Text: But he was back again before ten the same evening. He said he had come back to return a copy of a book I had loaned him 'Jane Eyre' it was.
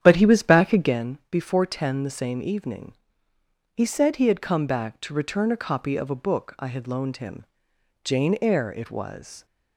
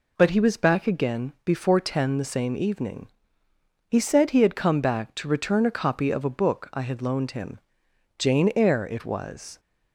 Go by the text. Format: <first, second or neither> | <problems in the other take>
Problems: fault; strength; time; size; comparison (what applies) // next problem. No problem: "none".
second | starts louder than the rest; strong; until 1.1 s; 9.5 dB // pauses between "him" and "Jane"; noticeable; at 7.4 s; 0.58 s long; noticeable in the second